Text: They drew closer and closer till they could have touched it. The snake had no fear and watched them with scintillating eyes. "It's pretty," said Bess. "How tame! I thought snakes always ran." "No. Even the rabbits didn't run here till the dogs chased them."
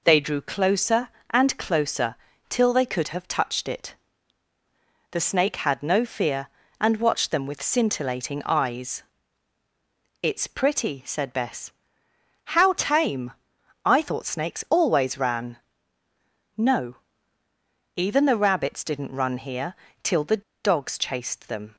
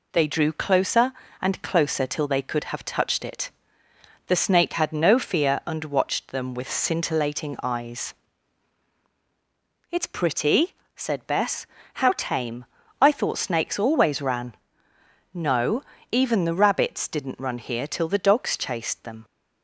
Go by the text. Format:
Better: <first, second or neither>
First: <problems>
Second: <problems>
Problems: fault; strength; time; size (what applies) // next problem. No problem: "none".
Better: second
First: pauses between "closer" and "till"; slight; at 2.1 s; 0.32 s long // pauses between "here" and "till"; slight; at 19.7 s; 0.28 s long // pauses between "the" and "dogs"; slight; at 20.4 s; 0.22 s long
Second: none